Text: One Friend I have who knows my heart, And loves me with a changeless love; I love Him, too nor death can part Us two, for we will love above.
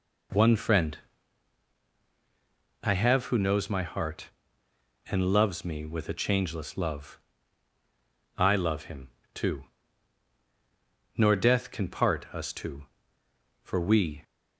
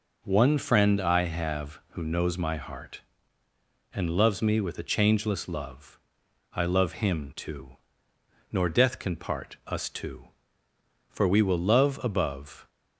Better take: second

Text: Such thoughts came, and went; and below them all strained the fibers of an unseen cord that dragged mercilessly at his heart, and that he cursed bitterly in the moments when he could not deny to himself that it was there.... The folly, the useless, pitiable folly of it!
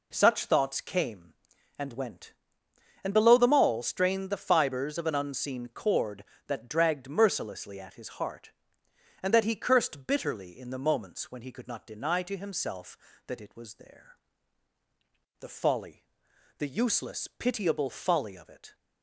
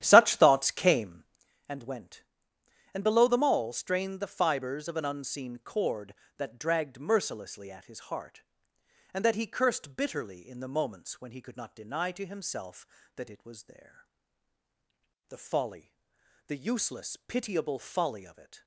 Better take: first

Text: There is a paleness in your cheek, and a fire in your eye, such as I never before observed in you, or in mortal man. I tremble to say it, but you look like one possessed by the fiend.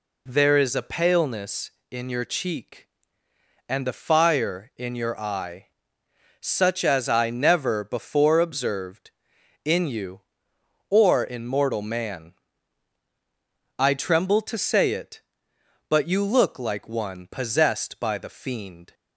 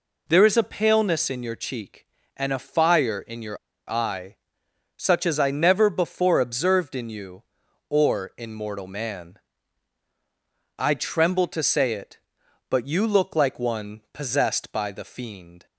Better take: first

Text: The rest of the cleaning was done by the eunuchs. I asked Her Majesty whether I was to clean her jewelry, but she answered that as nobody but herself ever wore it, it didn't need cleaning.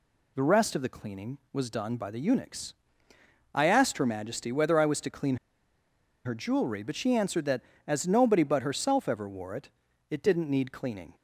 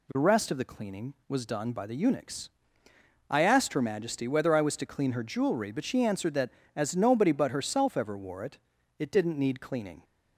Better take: second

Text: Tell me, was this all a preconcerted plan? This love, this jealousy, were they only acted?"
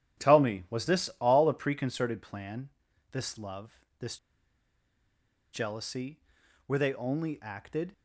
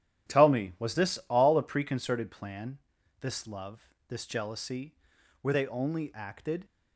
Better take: second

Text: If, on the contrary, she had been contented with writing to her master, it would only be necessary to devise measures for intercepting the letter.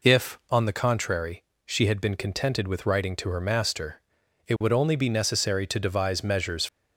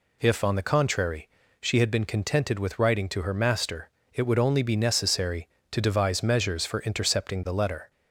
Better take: second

